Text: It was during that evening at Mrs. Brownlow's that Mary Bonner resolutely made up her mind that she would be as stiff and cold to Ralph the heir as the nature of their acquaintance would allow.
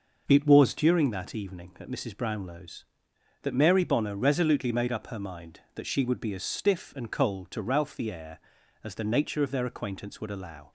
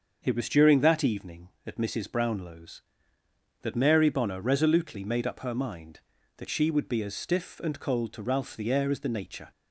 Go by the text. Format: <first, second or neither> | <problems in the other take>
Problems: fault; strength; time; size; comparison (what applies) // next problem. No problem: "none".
first | starts louder than the rest; until 1.2 s; 7 dB // stops before "of their acquaintance would allow"; at 9.5 s